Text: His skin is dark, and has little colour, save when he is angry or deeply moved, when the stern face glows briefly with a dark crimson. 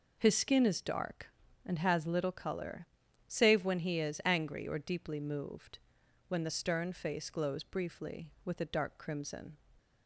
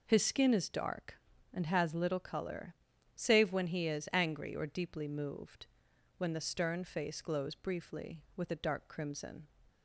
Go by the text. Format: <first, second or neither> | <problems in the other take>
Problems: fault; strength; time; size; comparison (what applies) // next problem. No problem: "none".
neither | none